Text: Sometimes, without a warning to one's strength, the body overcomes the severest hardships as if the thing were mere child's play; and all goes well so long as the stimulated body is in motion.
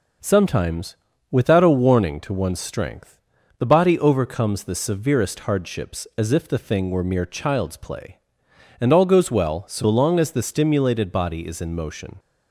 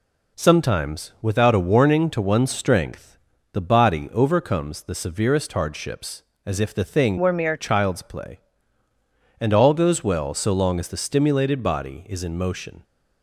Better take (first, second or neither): first